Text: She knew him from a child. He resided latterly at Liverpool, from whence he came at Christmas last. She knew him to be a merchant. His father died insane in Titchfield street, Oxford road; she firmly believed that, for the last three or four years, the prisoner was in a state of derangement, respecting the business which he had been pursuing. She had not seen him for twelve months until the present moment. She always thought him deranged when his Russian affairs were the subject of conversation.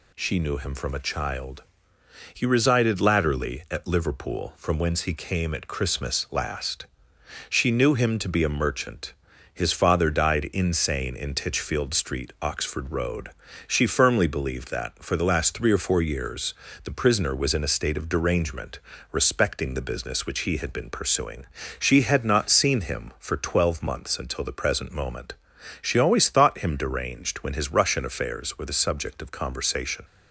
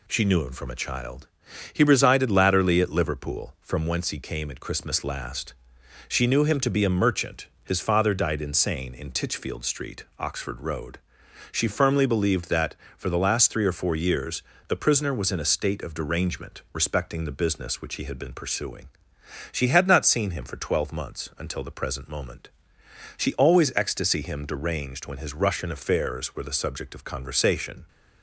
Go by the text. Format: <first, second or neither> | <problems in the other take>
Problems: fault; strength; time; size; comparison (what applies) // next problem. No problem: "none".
first | says "ecstasy" for "thought"; at 23.7 s